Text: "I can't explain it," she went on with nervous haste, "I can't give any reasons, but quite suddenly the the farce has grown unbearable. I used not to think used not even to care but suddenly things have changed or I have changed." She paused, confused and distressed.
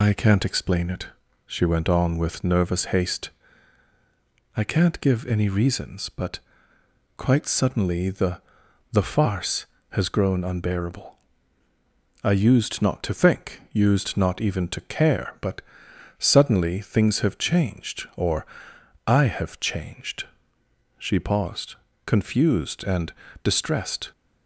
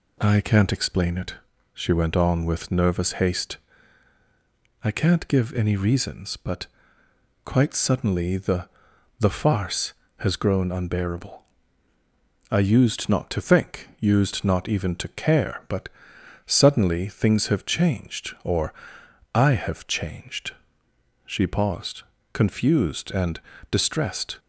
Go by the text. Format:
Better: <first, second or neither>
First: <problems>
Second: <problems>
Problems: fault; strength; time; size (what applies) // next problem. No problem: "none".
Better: second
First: loses the start of "I"; at 0.0 s; 80 ms // pauses between "but" and "quite"; noticeable; at 6.3 s; 0.78 s long // pauses between "the" and "the"; noticeable; at 8.4 s; 0.52 s long // pauses between "but" and "suddenly"; noticeable; at 15.5 s; 0.58 s long // pauses between "or" and "I"; noticeable; at 18.4 s; 0.60 s long // pauses between "and" and "distressed"; slight; at 23.1 s; 0.32 s long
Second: pauses between "but" and "quite"; noticeable; at 6.6 s; 0.78 s long // pauses between "the" and "the"; noticeable; at 8.6 s; 0.52 s long // pauses between "but" and "suddenly"; noticeable; at 15.8 s; 0.58 s long // pauses between "or" and "I"; noticeable; at 18.7 s; 0.60 s long // pauses between "and" and "distressed"; slight; at 23.3 s; 0.32 s long